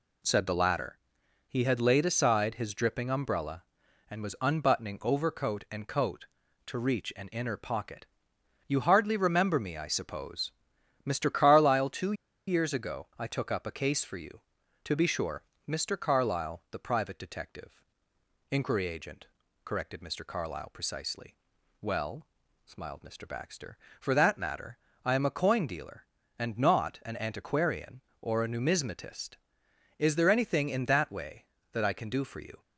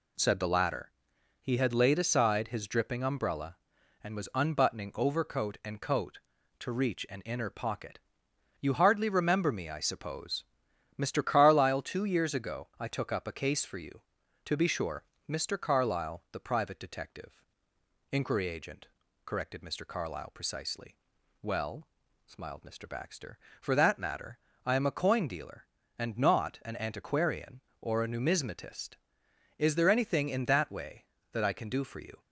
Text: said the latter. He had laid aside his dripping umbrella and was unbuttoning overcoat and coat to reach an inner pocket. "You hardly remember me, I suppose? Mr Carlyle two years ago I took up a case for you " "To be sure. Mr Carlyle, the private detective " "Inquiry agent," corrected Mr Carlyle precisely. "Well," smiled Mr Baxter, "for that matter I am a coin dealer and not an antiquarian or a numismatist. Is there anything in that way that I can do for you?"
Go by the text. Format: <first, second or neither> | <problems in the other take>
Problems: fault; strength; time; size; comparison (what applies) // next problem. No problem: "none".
second | pauses between "two" and "years"; slight; at 12.1 s; 0.34 s long // pauses between "matter" and "I"; slight; at 24.7 s; 0.28 s long; slight in the second